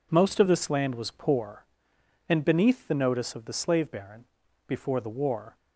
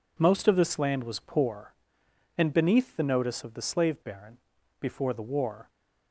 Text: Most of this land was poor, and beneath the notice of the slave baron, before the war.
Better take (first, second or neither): neither